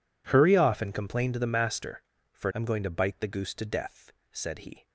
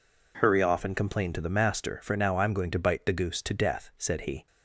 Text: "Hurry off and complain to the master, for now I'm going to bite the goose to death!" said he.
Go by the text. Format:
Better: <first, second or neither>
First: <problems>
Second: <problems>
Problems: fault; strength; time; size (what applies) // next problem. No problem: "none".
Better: second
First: skips "now"; at 2.5 s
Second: none